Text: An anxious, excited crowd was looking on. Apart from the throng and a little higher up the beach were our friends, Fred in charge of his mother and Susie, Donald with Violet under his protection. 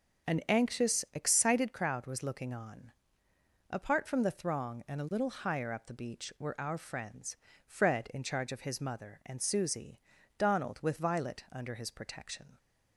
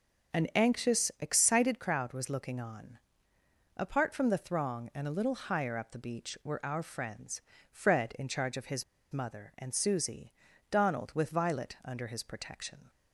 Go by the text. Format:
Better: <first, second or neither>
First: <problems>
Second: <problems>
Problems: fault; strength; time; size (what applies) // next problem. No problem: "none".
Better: first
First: starts louder than the rest; until 1.4 s; 6 dB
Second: starts louder than the rest; until 1.4 s; 6 dB // pauses between "his" and "mother"; slight; at 8.8 s; 0.28 s long